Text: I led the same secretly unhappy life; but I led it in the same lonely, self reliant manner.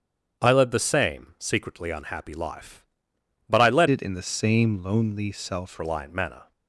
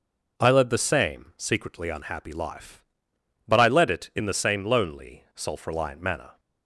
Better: second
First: starts louder than the rest; strong; until 1.4 s; 8 dB // changes voice from "it" to "self"; from 3.9 to 5.8 s; 1.9 s long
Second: none

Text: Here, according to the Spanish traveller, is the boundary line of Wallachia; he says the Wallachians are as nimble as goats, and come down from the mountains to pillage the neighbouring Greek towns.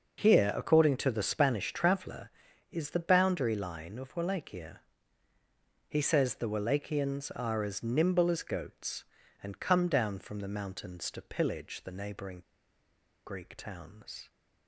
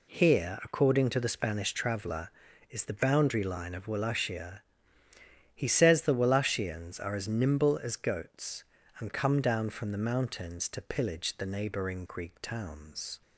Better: second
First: pauses between "neighbouring" and "Greek"; noticeable; at 12.4 s; 0.85 s long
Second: none

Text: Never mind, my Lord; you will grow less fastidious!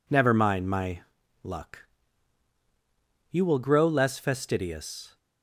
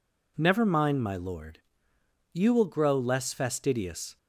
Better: second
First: says "Luck" for "Lord"; at 1.4 s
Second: none

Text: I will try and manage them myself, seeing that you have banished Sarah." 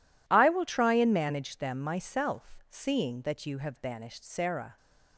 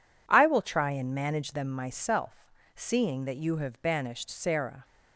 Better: neither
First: none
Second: none

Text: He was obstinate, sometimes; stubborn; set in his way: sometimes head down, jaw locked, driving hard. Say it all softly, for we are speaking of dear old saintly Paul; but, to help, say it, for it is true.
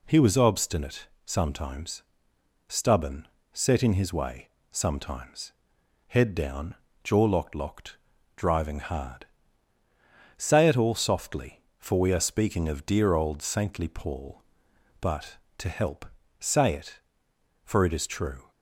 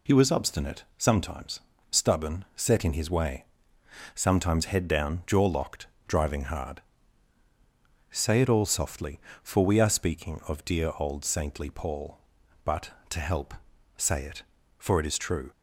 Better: second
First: pauses between "sometimes" and "head"; noticeable; at 5.5 s; 0.56 s long // says "locked" twice; at 7.5 s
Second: none

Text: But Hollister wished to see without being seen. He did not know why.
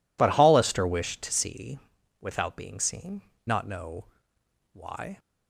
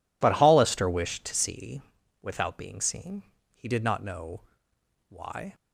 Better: second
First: pauses between "see" and "without"; at 1.7 s; 0.42 s long // skips "He did"; at 3.3 s // pauses between "know" and "why"; noticeable; at 4.0 s; 0.66 s long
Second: pauses between "see" and "without"; at 1.8 s; 0.40 s long // pauses between "know" and "why"; noticeable; at 4.4 s; 0.66 s long

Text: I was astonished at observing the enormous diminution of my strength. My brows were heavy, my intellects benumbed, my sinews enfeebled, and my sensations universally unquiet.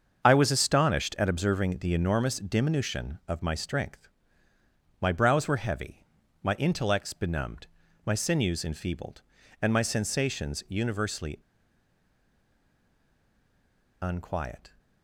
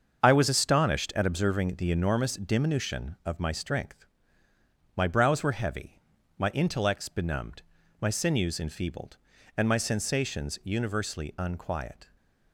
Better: second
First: starts louder than the rest; until 1.2 s; 7 dB // pauses between "universally" and "unquiet"; strong; at 11.3 s; 2.6 s long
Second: starts louder than the rest; until 1.2 s; 7 dB

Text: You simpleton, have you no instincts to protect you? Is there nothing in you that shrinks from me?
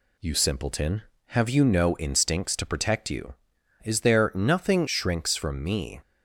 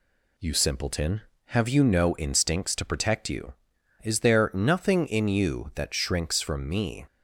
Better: second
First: skips "in you that"; at 4.8 s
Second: none

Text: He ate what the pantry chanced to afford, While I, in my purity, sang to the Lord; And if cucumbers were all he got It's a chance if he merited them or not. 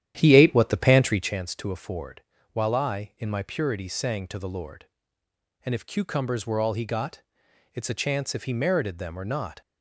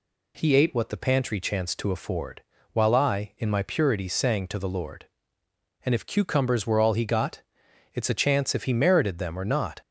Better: second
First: starts louder than the rest; strong; until 1.4 s; 10.5 dB // pauses between "got" and "It's"; noticeable; at 7.1 s; 0.54 s long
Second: pauses between "got" and "It's"; noticeable; at 7.3 s; 0.54 s long

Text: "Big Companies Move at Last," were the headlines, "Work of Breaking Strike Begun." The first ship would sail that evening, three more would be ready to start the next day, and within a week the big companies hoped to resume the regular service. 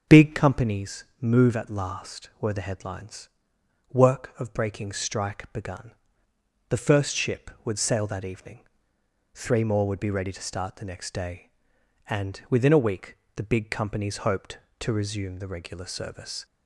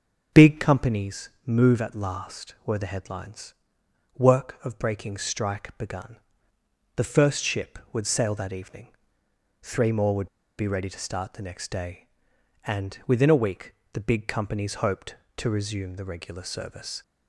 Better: first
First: starts louder than the rest; until 1.2 s; 6 dB // pauses between "Companies" and "Move"; slight; at 1.0 s; 0.16 s long // pauses between "week" and "the"; slight; at 13.1 s; 0.20 s long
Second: starts louder than the rest; until 1.5 s; 6 dB // pauses between "Companies" and "Move"; slight; at 1.2 s; 0.16 s long // pauses between "would" and "be"; slight; at 10.2 s; 0.31 s long // pauses between "week" and "the"; slight; at 13.7 s; 0.20 s long

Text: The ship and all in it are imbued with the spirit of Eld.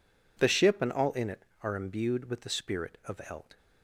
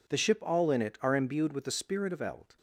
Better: first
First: none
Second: skips "and"; at 0.3 s

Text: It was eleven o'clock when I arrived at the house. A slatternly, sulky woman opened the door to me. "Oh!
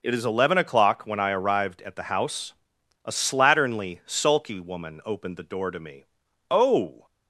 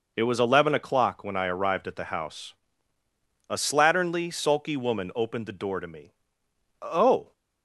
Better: second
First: says "is" for "was"; at 0.1 s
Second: none

